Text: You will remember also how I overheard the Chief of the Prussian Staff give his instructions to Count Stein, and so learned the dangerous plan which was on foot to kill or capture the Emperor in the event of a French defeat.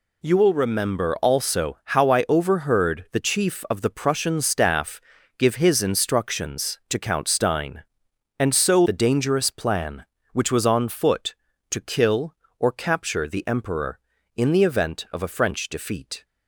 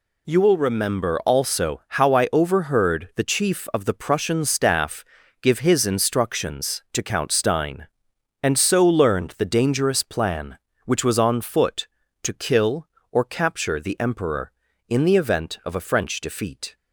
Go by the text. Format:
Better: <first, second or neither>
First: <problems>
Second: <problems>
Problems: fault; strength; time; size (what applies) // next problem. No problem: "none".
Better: second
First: pauses between "Staff" and "give"; at 5.0 s; 0.38 s long // skips "learned"; at 8.8 s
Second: pauses between "Staff" and "give"; at 5.0 s; 0.38 s long